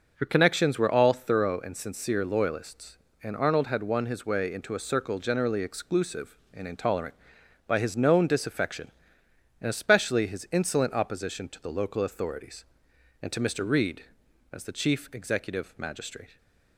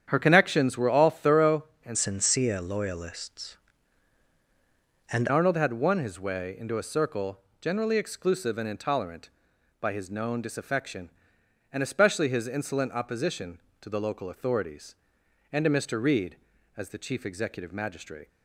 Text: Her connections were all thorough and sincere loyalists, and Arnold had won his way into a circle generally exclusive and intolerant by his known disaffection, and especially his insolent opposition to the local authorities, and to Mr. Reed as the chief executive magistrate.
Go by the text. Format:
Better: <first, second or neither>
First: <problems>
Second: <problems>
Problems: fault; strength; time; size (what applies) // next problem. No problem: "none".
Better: first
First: starts louder than the rest; until 1.1 s; 6 dB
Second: starts louder than the rest; strong; until 1.0 s; 8.5 dB // changes voice from "sincere" to "and"; from 1.9 to 5.2 s; 3.3 s long // pauses between "circle" and "generally"; slight; at 7.3 s; 0.22 s long